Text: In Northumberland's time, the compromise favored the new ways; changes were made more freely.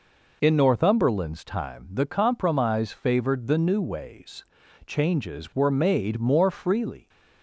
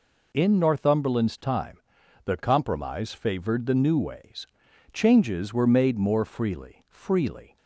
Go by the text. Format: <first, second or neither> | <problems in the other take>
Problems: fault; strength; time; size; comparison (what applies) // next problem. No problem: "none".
first | says "freely" twice; at 6.8 s